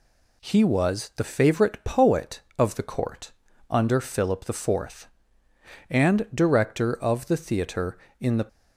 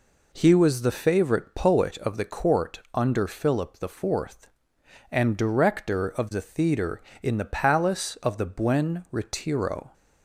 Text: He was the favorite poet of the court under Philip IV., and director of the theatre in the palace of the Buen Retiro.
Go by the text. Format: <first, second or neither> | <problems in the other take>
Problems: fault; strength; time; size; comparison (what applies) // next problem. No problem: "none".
second | pauses between "court" and "under"; at 3.3 s; 0.38 s long; slight in the second // stops before "palace of the Buen Retiro"; at 8.4 s